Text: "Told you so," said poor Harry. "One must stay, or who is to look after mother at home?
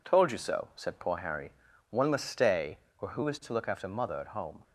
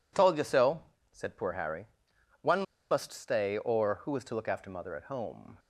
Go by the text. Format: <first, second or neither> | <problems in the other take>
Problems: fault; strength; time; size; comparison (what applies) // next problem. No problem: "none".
first | pauses between "One" and "must"; slight; at 2.6 s; 0.28 s long